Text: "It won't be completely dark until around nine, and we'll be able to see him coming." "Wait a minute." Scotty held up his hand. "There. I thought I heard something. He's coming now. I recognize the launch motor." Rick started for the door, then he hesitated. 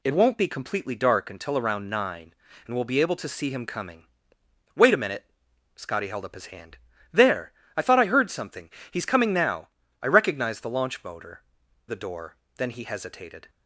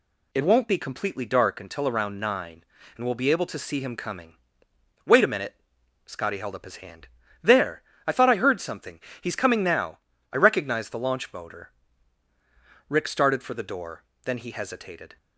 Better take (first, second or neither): second